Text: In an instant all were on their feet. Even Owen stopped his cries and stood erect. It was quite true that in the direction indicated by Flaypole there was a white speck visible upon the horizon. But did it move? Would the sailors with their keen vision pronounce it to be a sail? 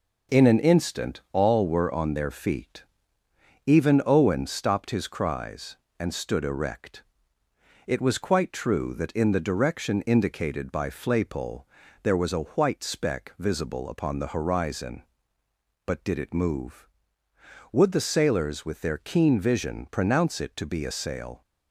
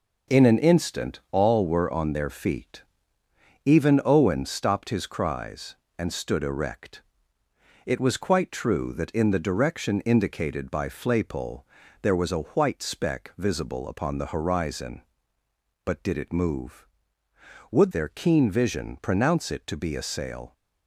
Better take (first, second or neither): first